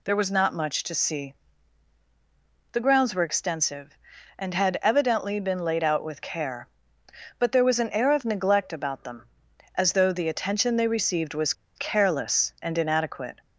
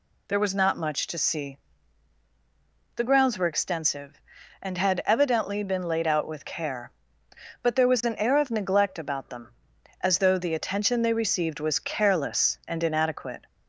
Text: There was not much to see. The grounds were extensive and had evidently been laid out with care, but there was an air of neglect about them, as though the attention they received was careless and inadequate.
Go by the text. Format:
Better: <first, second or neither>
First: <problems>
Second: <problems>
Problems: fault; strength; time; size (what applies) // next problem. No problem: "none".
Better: second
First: pauses between "was" and "careless"; slight; at 11.5 s; 0.23 s long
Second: none